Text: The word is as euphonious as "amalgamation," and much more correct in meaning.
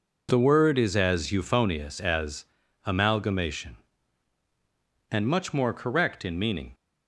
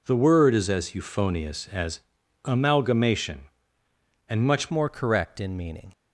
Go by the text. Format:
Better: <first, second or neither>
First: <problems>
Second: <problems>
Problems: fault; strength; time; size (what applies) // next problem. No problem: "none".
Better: first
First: pauses between "as" and "amalgamation"; at 2.4 s; 0.40 s long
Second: pauses between "as" and "amalgamation"; at 2.0 s; 0.42 s long // changes voice at "more"; from 4.6 s on; 1.3 s long